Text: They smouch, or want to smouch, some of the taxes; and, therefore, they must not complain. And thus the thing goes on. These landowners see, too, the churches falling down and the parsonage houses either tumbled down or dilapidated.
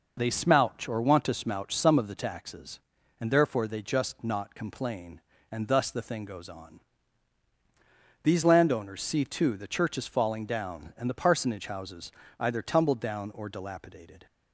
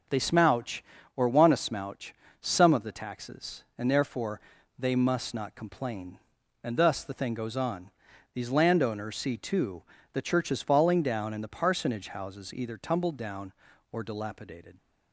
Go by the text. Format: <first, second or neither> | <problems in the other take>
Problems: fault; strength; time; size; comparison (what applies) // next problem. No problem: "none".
second | says "just" for "must"; at 3.8 s // pauses between "houses" and "either"; slight; at 12.1 s; 0.28 s long